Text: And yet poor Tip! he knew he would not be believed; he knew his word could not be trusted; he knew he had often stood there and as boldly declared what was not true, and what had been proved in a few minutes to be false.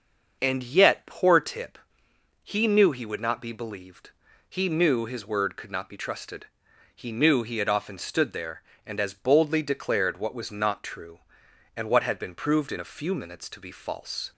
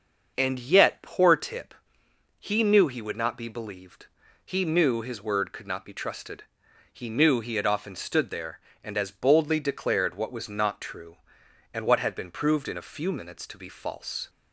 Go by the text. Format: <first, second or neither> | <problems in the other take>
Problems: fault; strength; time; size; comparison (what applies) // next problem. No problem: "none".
neither | starts louder than the rest; the same in both